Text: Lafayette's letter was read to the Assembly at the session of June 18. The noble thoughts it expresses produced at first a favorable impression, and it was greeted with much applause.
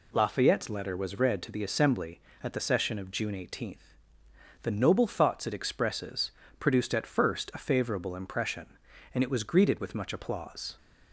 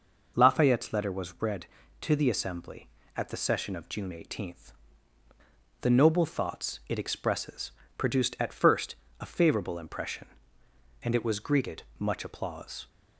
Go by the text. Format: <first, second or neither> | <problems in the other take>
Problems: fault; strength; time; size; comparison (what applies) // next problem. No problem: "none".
first | pauses between "expresses" and "produced"; slight; at 7.6 s; 0.28 s long; slight in the first // pauses between "first" and "a"; slight; at 8.9 s; 0.24 s long // skips "with"; at 11.9 s